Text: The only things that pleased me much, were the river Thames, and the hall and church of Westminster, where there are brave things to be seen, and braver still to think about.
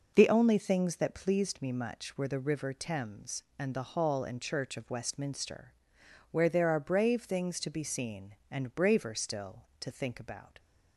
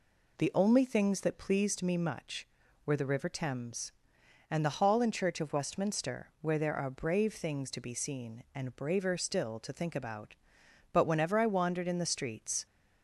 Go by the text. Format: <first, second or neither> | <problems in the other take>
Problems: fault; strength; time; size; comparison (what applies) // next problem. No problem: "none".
first | goes on to say "But whenever I wandered in the streets"; strong; from 10.9 s on; 1.7 s long